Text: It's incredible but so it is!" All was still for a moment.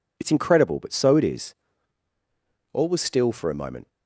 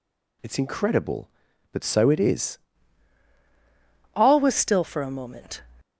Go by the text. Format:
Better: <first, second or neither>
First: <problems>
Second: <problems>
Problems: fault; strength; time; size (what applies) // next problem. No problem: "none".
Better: first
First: none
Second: changes voice at "All"; from 4.1 s on; 1.5 s long